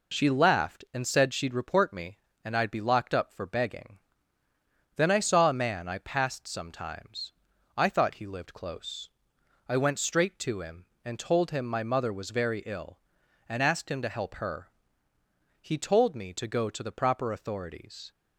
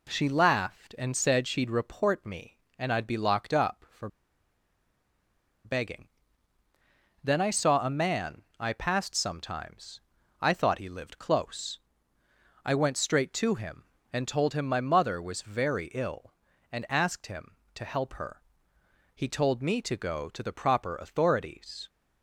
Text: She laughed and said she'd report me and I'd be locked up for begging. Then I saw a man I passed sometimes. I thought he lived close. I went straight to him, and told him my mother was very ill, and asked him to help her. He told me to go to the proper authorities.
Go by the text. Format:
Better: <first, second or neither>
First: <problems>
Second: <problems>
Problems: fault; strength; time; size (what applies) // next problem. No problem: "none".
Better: first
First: none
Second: pauses between "for" and "begging"; strong; at 4.0 s; 1.5 s long // pauses between "man" and "I"; slight; at 8.4 s; 0.16 s long